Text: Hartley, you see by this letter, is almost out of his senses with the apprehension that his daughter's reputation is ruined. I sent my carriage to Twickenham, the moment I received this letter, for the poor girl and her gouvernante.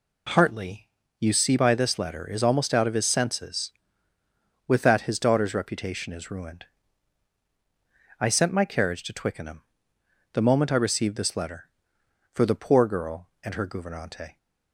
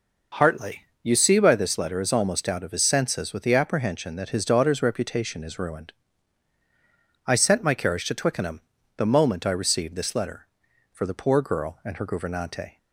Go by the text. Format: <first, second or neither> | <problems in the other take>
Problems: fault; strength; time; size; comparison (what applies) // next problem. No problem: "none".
second | skips "the apprehension"; at 4.8 s